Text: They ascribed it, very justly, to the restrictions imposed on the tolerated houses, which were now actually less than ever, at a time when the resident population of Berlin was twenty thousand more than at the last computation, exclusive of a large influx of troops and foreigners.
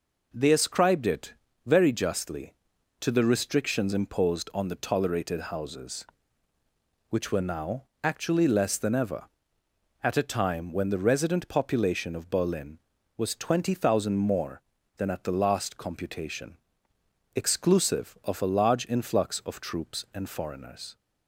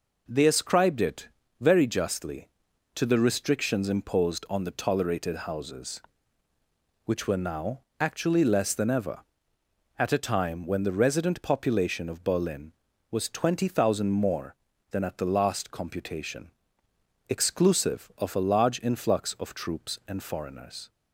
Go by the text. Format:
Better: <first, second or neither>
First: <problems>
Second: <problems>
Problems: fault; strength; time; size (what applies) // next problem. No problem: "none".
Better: neither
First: pauses between "now" and "actually"; slight; at 7.8 s; 0.20 s long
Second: pauses between "now" and "actually"; slight; at 7.7 s; 0.20 s long